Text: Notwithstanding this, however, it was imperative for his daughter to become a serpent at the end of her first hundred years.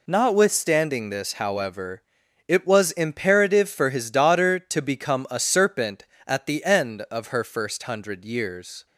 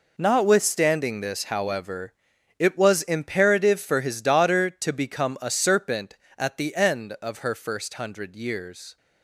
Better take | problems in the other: first | gets quieter; strong; throughout; 12.5 dB

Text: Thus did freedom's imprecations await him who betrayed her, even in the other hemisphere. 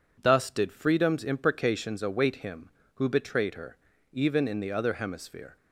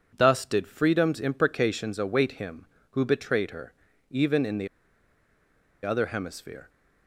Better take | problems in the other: first | pauses between "the" and "other"; at 4.6 s; 1.1 s long

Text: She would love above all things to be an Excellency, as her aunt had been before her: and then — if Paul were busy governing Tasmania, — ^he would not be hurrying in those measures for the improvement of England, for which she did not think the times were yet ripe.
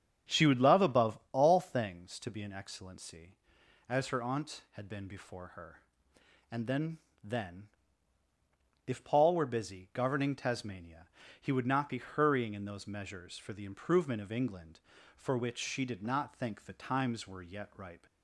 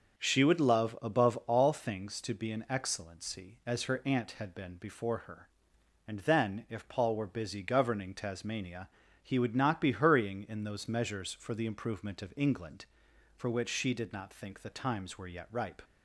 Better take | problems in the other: second | starts louder than the rest; strong; until 1.4 s; 8.5 dB; noticeable in the second // says "then" twice; at 7.2 s

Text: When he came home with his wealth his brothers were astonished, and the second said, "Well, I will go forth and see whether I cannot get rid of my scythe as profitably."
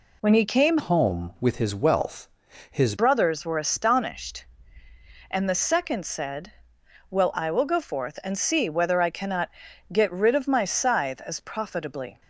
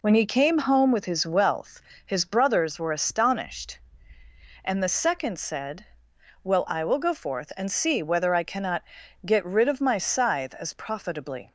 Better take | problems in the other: second | changes voice from "home" to "his"; from 0.7 to 2.9 s; 2.2 s long // pauses between "wealth" and "his"; at 2.2 s; 0.42 s long; slight in the second // pauses between "cannot" and "get"; at 9.5 s; 0.40 s long; also in the second

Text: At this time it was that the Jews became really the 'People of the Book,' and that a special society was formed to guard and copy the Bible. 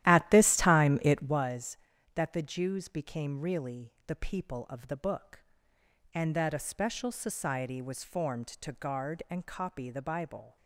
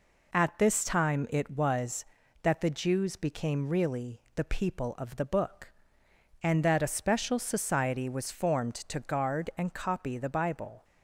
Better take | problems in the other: second | starts louder than the rest; strong; until 1.5 s; 13 dB

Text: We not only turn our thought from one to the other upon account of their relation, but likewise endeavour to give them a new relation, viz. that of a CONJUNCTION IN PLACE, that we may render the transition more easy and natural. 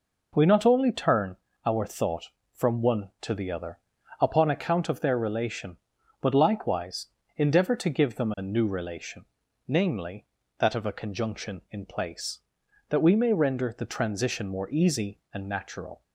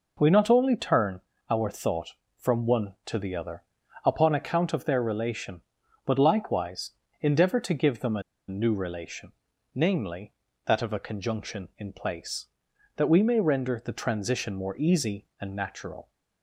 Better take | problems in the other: first | pauses between "turn" and "our"; slight; at 1.2 s; 0.28 s long; slight in the first // pauses between "other" and "upon"; at 3.6 s; 0.42 s long; also in the first // pauses between "likewise" and "endeavour"; slight; at 6.9 s; 0.30 s long; slight in the first // pauses between "a" and "new"; slight; at 8.2 s; 0.27 s long

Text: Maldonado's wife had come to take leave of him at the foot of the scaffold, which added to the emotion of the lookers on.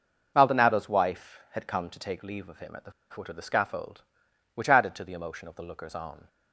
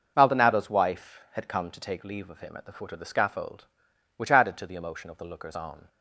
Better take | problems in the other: second | pauses between "the" and "foot"; slight; at 2.9 s; 0.18 s long

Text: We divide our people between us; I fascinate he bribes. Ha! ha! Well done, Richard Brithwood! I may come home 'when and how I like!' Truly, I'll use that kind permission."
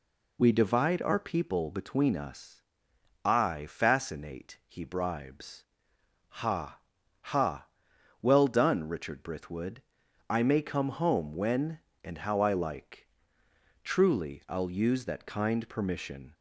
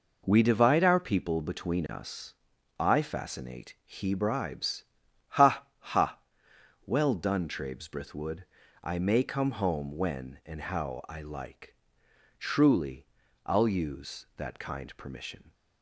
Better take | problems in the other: first | says "Trabes" for "Richard"; at 7.4 s

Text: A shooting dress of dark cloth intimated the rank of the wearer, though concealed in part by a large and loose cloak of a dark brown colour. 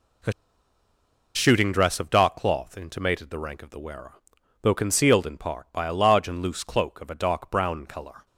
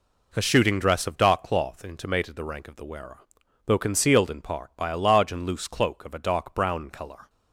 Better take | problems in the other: second | pauses between "A" and "shooting"; at 0.3 s; 1.0 s long

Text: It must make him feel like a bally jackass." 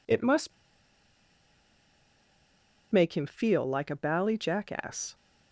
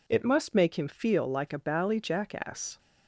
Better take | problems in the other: second | pauses between "must" and "make"; strong; at 0.5 s; 2.4 s long

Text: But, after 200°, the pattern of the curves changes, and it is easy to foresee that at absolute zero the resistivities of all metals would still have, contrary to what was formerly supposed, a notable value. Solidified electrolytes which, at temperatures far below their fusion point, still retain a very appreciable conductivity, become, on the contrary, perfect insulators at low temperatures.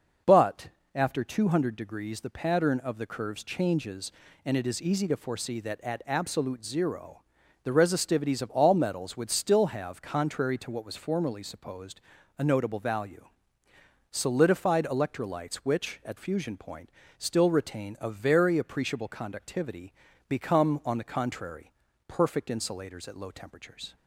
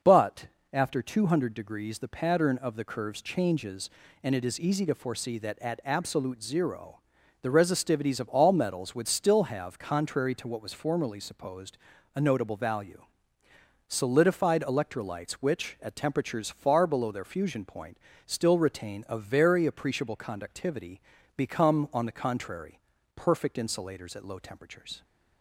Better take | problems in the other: second | starts louder than the rest; until 1.5 s; 6 dB; noticeable in the second // pauses between "zero" and "the"; at 7.2 s; 0.42 s long; also in the second // skips "temperatures far below their"; at 16.1 s

